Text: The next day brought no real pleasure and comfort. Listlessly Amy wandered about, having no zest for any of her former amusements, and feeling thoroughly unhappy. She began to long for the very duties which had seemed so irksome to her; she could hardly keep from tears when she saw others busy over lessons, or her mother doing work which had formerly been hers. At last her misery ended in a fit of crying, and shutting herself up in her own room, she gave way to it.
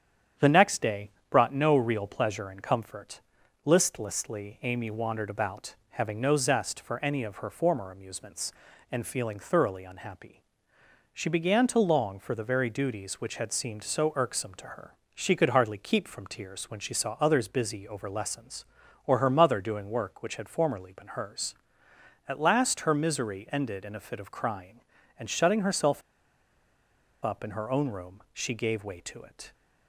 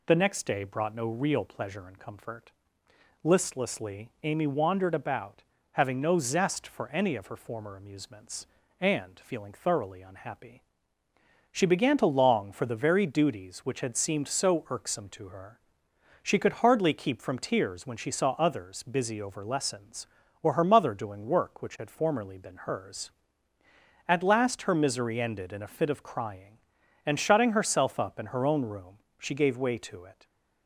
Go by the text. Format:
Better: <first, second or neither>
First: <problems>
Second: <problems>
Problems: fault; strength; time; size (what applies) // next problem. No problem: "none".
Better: second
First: starts louder than the rest; strong; until 1.5 s; 9 dB // pauses between "day" and "brought"; slight; at 1.1 s; 0.18 s long // pauses between "herself" and "up"; at 26.0 s; 1.2 s long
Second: none